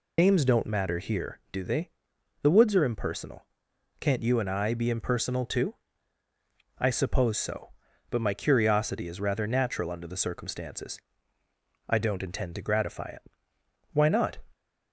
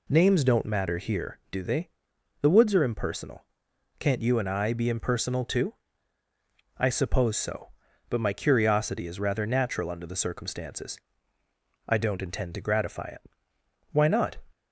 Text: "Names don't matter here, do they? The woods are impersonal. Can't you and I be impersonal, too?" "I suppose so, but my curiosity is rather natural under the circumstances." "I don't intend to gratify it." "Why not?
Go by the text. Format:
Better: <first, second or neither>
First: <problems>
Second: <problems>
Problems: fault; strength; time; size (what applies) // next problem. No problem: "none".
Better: second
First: loses the start of "Names"; at 0.1 s; 85 ms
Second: none